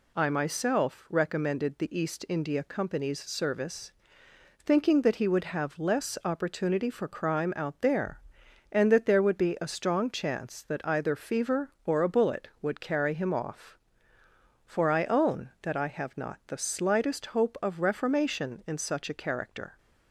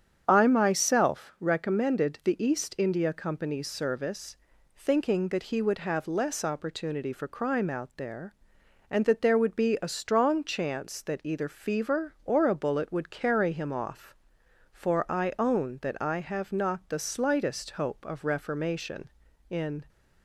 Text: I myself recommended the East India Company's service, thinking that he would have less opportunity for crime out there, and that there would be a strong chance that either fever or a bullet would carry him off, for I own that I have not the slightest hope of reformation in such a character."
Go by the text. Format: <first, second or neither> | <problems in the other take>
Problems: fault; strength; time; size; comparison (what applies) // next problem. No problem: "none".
first | starts louder than the rest; strong; until 1.2 s; 8 dB // stops before "such a character"; at 19.8 s